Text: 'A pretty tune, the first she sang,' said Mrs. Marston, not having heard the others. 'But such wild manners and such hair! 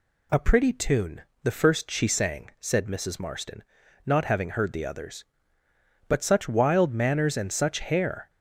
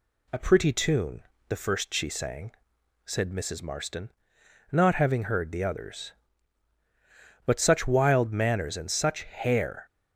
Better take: neither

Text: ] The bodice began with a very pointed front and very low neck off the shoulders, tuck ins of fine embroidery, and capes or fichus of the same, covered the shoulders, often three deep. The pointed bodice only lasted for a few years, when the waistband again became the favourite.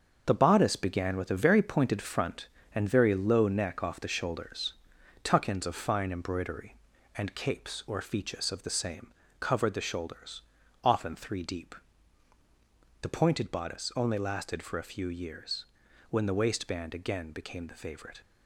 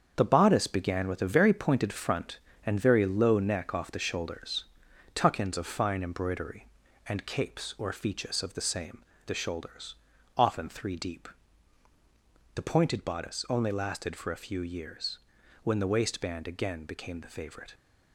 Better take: first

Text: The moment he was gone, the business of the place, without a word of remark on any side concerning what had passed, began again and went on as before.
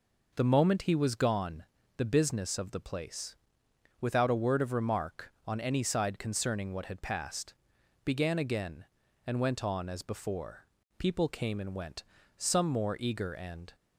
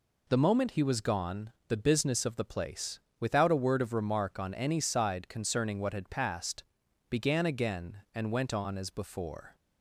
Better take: second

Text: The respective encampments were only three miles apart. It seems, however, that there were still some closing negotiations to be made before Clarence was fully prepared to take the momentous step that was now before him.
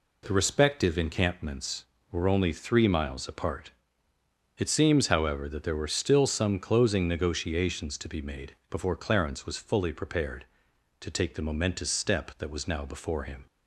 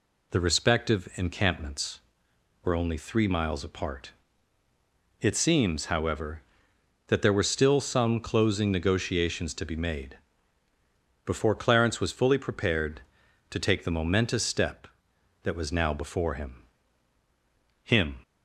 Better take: first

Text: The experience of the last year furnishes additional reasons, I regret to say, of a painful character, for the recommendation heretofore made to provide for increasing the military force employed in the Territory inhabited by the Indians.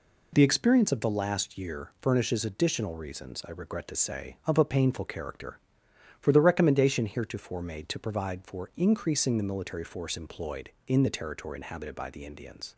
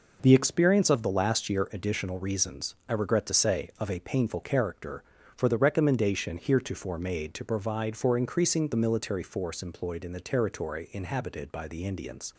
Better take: first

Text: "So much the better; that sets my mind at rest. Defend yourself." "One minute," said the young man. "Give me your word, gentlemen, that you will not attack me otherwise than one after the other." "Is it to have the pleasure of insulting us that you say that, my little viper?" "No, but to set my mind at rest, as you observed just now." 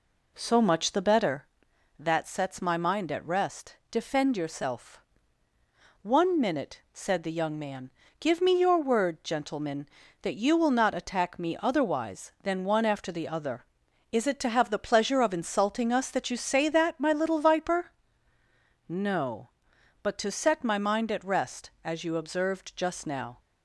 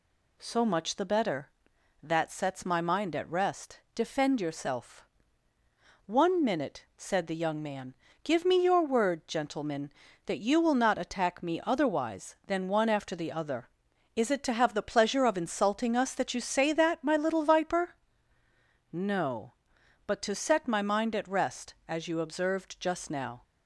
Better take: second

